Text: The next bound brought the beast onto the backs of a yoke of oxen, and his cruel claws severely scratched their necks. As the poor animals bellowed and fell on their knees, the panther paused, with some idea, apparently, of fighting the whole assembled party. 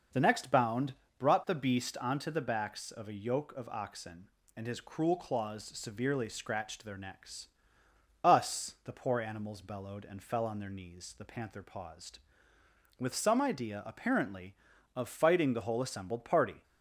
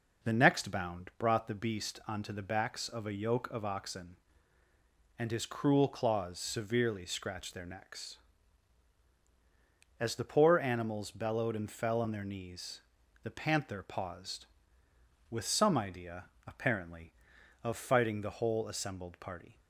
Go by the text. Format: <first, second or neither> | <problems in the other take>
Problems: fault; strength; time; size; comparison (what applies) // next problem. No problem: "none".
second | starts louder than the rest; noticeable; until 1.3 s; 6 dB // pauses between "bound" and "brought"; slight; at 0.9 s; 0.26 s long // says "Us" for "As"; at 8.2 s